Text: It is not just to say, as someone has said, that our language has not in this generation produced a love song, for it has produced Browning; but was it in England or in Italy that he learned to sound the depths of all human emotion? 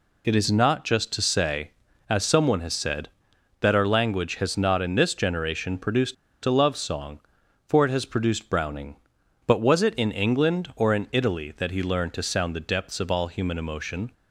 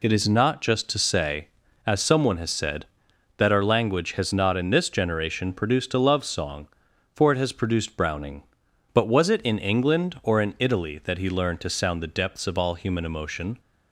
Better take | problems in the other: second | pauses between "produced" and "a"; slight; at 6.1 s; 0.29 s long

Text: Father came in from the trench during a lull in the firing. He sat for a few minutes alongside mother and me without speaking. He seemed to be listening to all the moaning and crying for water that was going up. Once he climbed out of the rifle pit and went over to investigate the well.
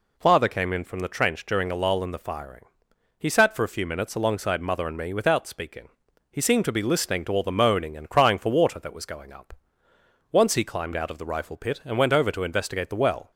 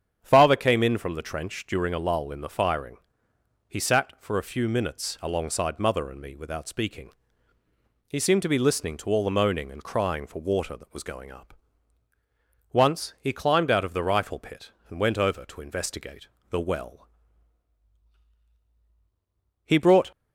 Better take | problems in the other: first | starts louder than the rest; strong; until 1.2 s; 8.5 dB // pauses between "investigate" and "the"; slight; at 16.2 s; 0.22 s long // goes on to say "He brought"; slight; from 19.6 s on; 0.46 s long

